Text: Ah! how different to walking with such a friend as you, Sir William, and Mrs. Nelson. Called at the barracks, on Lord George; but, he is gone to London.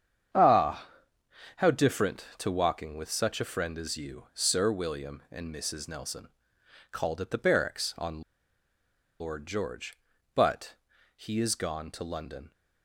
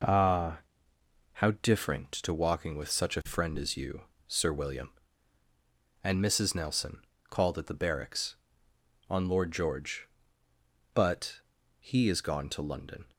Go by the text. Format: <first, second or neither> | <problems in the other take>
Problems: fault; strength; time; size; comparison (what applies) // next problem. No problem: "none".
second | starts louder than the rest; strong; until 2.0 s; 8 dB // pauses between "on" and "Lord"; at 8.2 s; 0.98 s long